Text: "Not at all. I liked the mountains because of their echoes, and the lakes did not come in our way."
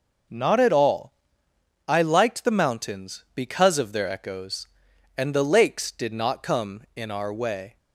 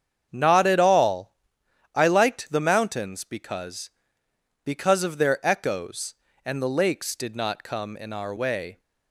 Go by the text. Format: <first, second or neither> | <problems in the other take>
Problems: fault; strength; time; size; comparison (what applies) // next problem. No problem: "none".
first | starts louder than the rest; strong; until 1.3 s; 8 dB // says "because" twice; at 4.6 s